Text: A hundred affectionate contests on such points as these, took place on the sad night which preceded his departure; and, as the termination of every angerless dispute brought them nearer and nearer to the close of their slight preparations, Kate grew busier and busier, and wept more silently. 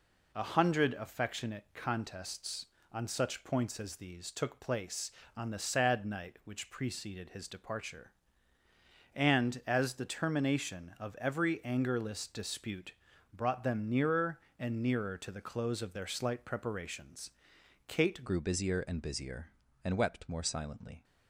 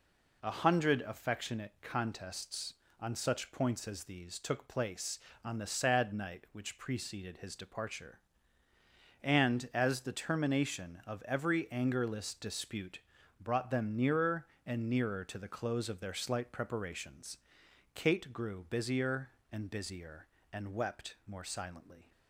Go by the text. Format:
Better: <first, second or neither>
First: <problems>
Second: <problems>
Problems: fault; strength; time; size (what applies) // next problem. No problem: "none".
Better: second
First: pauses between "dispute" and "brought"; at 12.9 s; 0.42 s long // changes voice at "grew"; from 18.2 s on; 2.8 s long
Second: pauses between "dispute" and "brought"; at 12.9 s; 0.42 s long